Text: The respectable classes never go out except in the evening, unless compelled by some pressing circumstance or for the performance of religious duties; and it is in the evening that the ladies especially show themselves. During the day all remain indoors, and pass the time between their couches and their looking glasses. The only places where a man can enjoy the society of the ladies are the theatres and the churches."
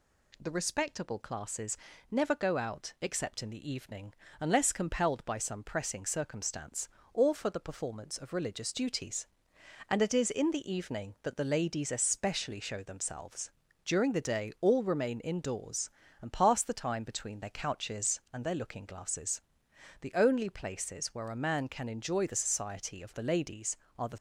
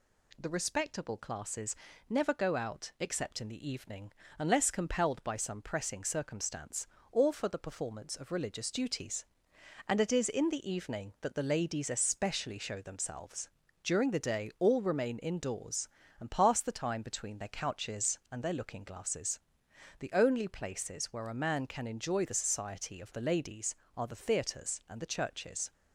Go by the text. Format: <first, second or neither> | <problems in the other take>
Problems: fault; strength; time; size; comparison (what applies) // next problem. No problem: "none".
second | pauses between "classes" and "never"; slight; at 1.7 s; 0.34 s long; slight in the second // stops before "theatres and the churches"; at 24.1 s